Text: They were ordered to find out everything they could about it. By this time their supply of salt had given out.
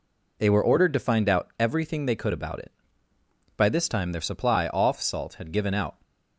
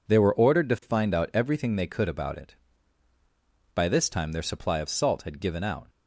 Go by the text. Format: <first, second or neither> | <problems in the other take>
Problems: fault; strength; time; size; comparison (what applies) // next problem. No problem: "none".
second | says "off" for "of"; at 4.6 s